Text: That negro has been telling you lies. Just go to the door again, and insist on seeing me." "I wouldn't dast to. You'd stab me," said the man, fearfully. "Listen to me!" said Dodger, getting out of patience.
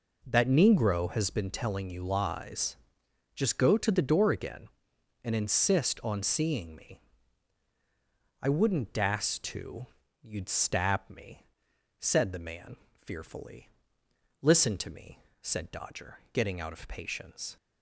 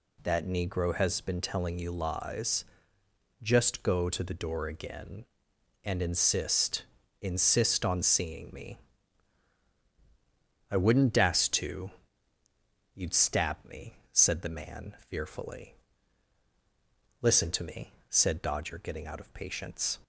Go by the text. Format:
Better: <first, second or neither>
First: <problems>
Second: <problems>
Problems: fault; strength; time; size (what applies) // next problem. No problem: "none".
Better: first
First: none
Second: says "insist" twice; at 7.2 s